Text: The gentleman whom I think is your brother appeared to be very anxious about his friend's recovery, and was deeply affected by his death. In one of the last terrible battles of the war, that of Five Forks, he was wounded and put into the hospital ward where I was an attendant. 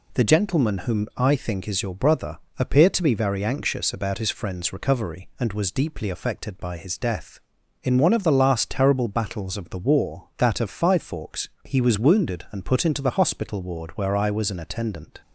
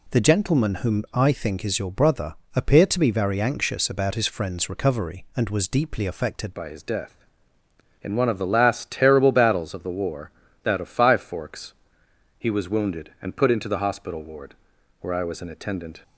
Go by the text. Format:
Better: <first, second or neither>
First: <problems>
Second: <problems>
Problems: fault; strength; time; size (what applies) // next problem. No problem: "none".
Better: first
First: pauses between "brother" and "appeared"; slight; at 2.3 s; 0.20 s long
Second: pauses between "brother" and "appeared"; slight; at 2.3 s; 0.20 s long // changes voice at "by"; from 6.5 s on; 9.5 s long // pauses between "ward" and "where"; noticeable; at 14.5 s; 0.48 s long